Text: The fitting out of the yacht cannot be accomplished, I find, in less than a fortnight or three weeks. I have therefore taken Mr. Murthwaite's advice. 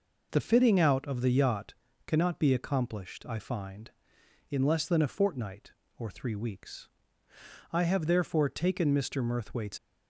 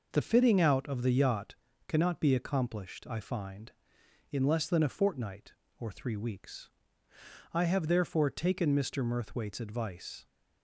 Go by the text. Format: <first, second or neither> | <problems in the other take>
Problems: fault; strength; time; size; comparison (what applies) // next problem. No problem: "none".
second | pauses between "yacht" and "cannot"; slight; at 1.7 s; 0.34 s long; slight in the second // stops before "advice"; at 9.7 s